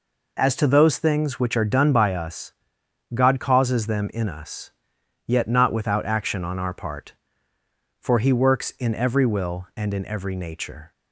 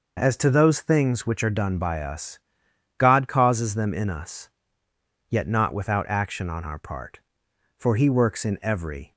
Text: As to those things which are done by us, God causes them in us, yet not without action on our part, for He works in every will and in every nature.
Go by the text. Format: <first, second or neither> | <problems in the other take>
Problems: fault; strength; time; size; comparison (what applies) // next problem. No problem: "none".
first | stops before "will and in every nature"; at 9.1 s